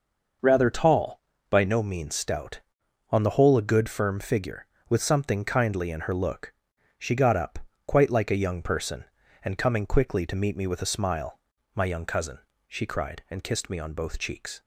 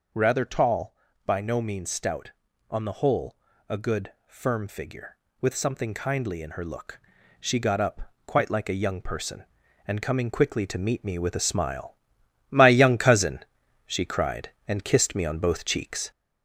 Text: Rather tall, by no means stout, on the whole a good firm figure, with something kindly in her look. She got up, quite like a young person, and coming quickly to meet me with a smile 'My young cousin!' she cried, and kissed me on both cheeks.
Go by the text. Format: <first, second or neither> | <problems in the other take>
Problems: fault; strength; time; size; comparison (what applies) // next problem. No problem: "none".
first | gets louder; throughout; 4 dB // pauses between "whole" and "a"; slight; at 3.3 s; 0.34 s long // pauses between "smile" and "My"; noticeable; at 11.9 s; 0.54 s long; slight in the first